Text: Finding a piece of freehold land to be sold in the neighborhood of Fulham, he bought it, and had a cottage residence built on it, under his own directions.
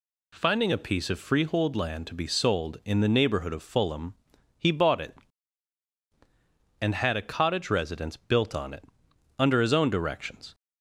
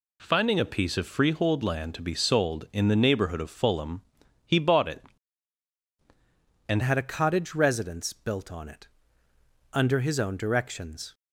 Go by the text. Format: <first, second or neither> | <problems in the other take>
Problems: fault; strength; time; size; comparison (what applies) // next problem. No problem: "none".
first | changes voice at "had"; from 6.8 s on; 4.3 s long